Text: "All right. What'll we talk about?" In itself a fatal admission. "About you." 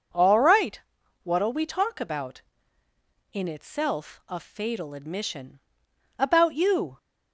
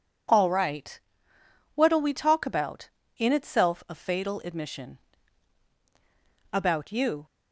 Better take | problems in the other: neither | none

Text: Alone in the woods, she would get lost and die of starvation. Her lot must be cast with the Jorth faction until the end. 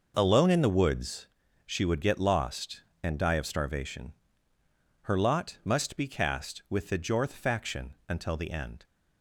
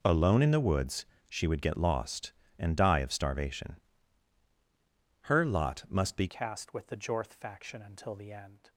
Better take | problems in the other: first | changes voice at "cast"; from 6.2 s on; 2.4 s long

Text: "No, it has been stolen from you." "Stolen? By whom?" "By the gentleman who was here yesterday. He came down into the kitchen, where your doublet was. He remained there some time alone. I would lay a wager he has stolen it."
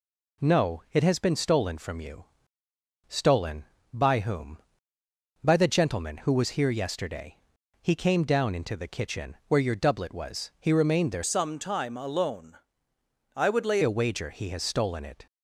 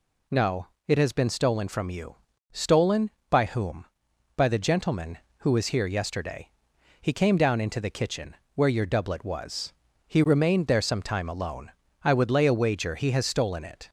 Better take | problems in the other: second | changes voice from "some" to "lay"; from 11.2 to 13.7 s; 2.5 s long

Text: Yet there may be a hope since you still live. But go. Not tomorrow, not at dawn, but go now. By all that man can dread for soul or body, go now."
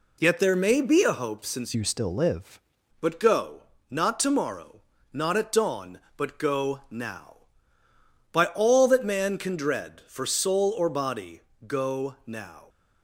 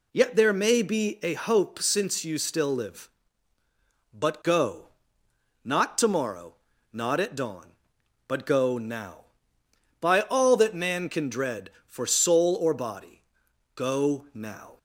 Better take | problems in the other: second | changes voice from "you" to "live"; from 1.7 to 2.5 s; 0.8 s long

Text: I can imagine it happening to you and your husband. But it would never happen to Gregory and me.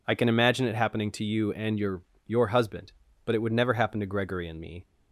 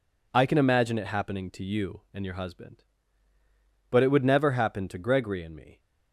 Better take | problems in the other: second | says "your" twice; at 2.2 s

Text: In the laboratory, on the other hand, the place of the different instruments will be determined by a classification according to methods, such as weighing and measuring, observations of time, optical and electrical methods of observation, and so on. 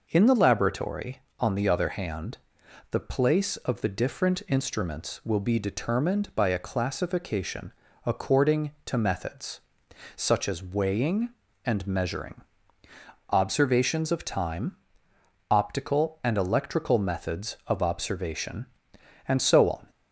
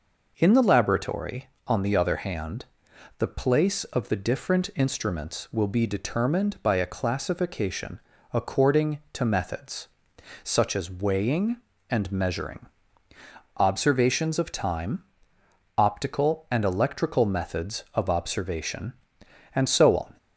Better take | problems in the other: neither | pauses between "classification" and "according"; slight; the same in both

